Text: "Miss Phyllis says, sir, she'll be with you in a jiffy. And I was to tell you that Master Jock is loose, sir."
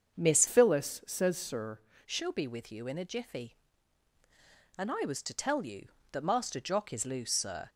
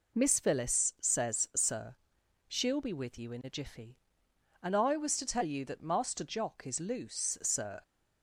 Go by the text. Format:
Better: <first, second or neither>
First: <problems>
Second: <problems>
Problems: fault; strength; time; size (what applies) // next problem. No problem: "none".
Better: second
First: starts louder than the rest; until 1.2 s; 7 dB // changes voice from "Phyllis" to "sir"; from 0.4 to 1.7 s; 1.3 s long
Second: none